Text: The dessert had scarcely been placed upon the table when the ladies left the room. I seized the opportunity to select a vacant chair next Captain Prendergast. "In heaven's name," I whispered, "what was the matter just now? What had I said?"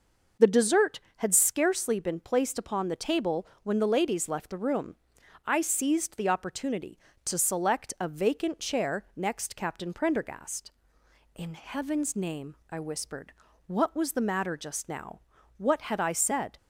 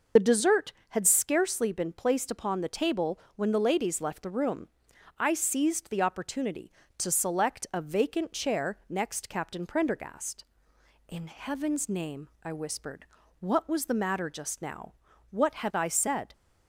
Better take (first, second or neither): first